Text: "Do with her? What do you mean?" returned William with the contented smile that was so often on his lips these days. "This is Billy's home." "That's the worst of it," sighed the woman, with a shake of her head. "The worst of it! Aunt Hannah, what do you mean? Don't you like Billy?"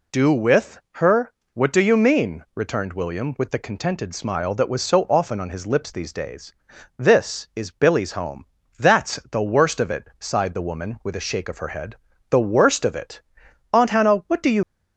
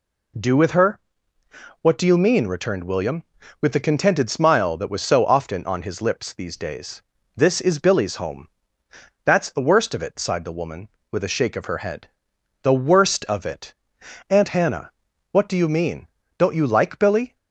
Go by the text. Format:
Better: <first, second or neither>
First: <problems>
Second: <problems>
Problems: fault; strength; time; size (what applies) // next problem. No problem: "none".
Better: second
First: pauses between "with" and "her"; slight; at 0.7 s; 0.24 s long // pauses between "That's" and "the"; slight; at 9.1 s; 0.16 s long // stops before "mean Don't you like Billy"; at 14.6 s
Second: none